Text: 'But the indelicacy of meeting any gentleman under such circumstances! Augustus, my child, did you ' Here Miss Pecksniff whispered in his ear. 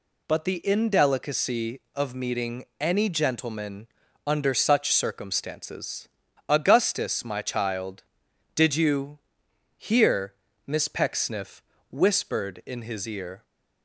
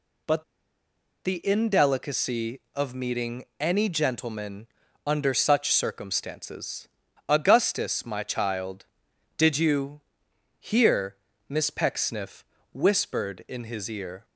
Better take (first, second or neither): first